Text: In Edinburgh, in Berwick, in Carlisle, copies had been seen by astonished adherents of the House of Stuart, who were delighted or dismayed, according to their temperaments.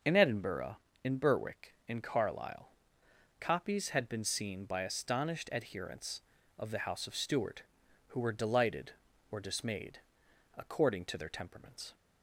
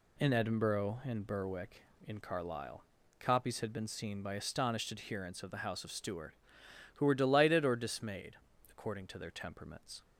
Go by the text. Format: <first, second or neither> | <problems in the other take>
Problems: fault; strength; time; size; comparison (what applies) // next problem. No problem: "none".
neither | none